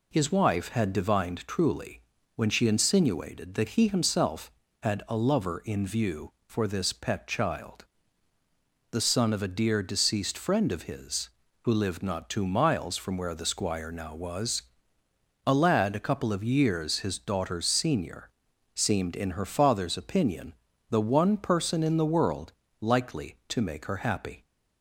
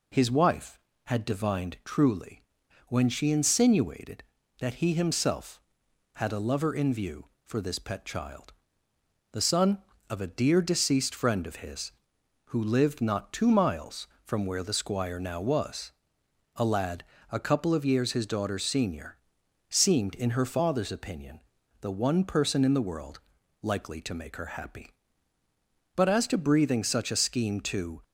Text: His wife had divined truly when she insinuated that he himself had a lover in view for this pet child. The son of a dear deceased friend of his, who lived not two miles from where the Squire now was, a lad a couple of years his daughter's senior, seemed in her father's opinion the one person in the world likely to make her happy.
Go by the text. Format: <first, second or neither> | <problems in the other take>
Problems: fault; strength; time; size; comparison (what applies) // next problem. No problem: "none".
first | pauses between "truly" and "when"; noticeable; at 2.4 s; 0.46 s long; slight in the first // pauses between "lad" and "a"; slight; at 17.0 s; 0.28 s long // pauses between "opinion" and "the"; at 21.4 s; 0.40 s long; also in the first // pauses between "world" and "likely"; at 23.1 s; 0.44 s long; slight in the first // goes on to say "But as to breathing such a scheme to"; strong; from 25.9 s on; 2.0 s long